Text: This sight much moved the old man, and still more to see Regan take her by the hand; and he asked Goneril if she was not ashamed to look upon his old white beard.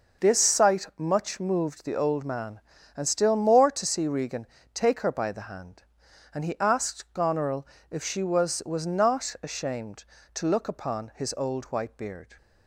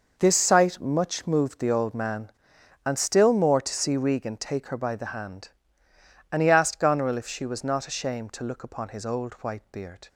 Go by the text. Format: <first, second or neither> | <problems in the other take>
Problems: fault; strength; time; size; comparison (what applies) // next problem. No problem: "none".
second | pauses between "Regan" and "take"; slight; at 4.4 s; 0.26 s long // pauses between "Goneril" and "if"; slight; at 7.6 s; 0.28 s long // says "was" twice; at 8.6 s